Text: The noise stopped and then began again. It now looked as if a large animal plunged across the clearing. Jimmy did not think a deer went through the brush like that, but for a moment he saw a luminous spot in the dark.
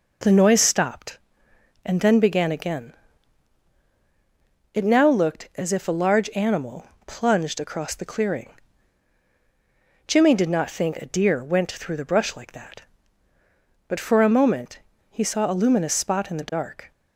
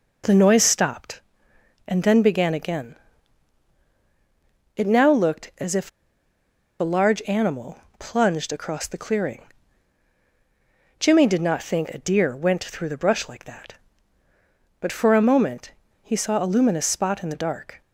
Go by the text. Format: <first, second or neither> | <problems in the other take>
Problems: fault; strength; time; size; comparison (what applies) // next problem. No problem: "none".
first | pauses between "if" and "a"; noticeable; at 5.8 s; 0.90 s long // pauses between "animal" and "plunged"; slight; at 7.7 s; 0.20 s long; slight in the first // pauses between "moment" and "he"; slight; at 15.7 s; 0.32 s long; slight in the first